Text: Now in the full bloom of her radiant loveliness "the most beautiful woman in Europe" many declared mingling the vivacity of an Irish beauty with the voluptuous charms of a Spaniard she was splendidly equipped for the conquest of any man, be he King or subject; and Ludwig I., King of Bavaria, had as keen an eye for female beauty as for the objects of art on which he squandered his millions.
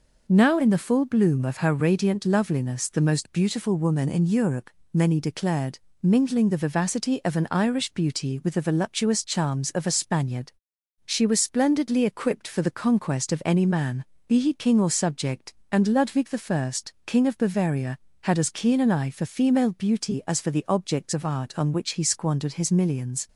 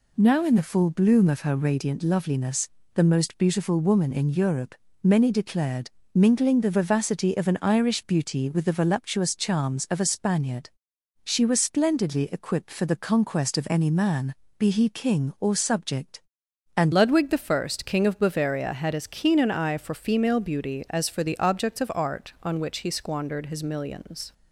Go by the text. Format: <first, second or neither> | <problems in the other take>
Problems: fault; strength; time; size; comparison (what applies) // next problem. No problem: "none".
first | pauses between "loveliness" and "the"; slight; at 2.6 s; 0.24 s long // pauses between "Europe" and "many"; slight; at 4.7 s; 0.26 s long; slight in the first // pauses between "declared" and "mingling"; slight; at 5.8 s; 0.24 s long; slight in the first // pauses between "Spaniard" and "she"; noticeable; at 10.6 s; 0.54 s long; noticeable in the first // changes voice at "Ludwig"; from 16.9 s on; 7.4 s long